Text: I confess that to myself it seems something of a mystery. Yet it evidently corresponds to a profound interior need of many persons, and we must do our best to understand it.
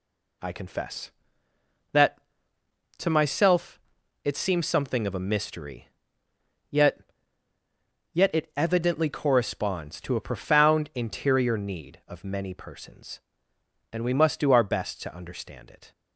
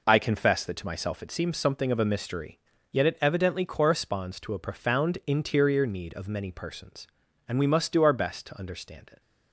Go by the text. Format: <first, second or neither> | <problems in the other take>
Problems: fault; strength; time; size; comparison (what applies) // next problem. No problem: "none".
second | pauses between "myself" and "it"; at 3.7 s; 0.44 s long // says "Yet" twice; at 8.1 s